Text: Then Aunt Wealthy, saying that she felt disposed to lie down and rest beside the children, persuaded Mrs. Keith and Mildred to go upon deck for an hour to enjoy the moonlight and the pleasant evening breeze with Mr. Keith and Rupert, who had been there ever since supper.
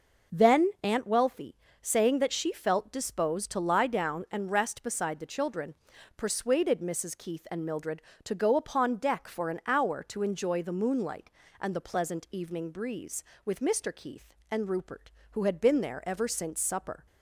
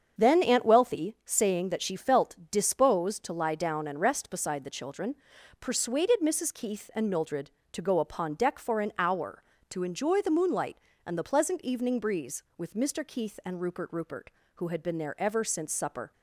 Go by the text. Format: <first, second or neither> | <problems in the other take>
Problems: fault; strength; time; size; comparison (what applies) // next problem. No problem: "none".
first | starts louder than the rest; strong; until 1.3 s; 7 dB // says "Rupert" twice; at 13.9 s